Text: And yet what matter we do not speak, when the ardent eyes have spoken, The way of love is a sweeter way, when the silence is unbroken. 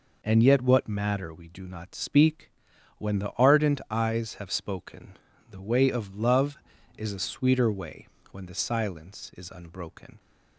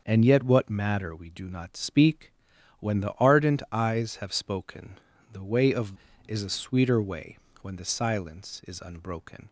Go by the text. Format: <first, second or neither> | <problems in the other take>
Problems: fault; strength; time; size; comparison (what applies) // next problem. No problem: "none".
first | starts louder than the rest; until 1.0 s; 6.5 dB // skips "love"; at 6.1 s